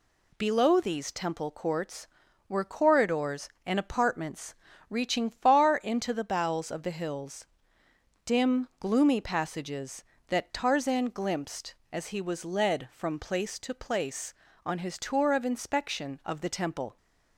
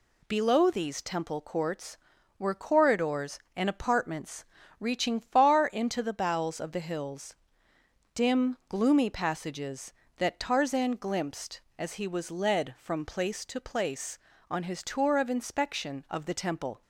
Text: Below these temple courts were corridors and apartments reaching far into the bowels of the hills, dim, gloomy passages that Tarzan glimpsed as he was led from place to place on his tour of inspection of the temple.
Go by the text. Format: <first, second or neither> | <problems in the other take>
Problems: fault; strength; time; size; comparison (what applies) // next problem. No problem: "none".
neither | pauses between "apartments" and "reaching"; slight; the same in both